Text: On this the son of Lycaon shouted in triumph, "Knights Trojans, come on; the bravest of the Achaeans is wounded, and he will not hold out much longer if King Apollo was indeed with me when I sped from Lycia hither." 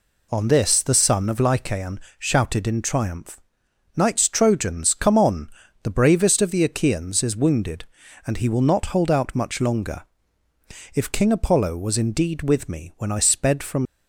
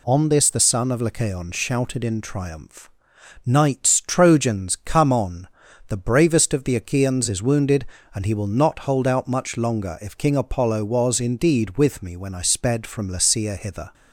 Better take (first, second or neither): second